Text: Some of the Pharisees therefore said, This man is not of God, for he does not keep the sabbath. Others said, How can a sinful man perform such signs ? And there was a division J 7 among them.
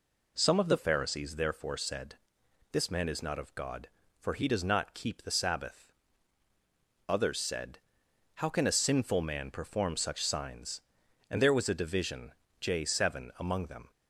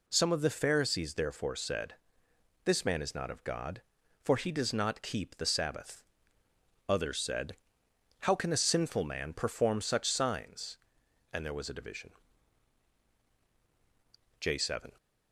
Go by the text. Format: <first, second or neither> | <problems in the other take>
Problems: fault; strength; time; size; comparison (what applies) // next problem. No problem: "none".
first | pauses between "division" and "J"; strong; at 12.1 s; 2.2 s long; slight in the first // stops before "among them"; at 14.9 s